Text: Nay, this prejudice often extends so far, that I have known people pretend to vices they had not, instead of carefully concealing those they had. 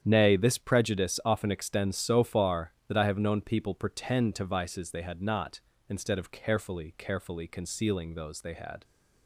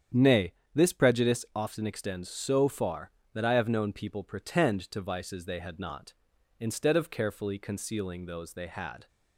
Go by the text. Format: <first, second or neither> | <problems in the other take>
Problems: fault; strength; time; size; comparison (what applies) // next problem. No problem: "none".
second | starts louder than the rest; strong; until 1.0 s; 9 dB; strong in the second // says "carefully" twice; at 6.9 s